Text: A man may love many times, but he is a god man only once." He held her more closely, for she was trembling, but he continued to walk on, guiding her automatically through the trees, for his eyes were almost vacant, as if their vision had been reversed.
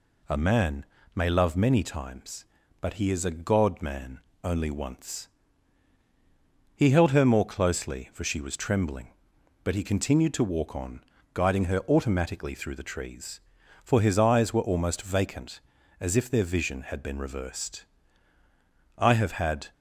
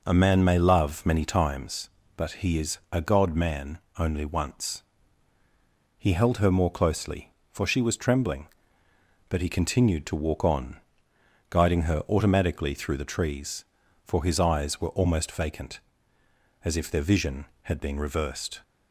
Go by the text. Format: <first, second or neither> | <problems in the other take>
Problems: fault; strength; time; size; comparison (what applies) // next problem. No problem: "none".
second | pauses between "man" and "may"; slight; at 0.8 s; 0.30 s long // pauses between "man" and "only"; slight; at 4.1 s; 0.24 s long; slight in the second // goes on to say "I have had"; noticeable; from 18.9 s on; 0.74 s long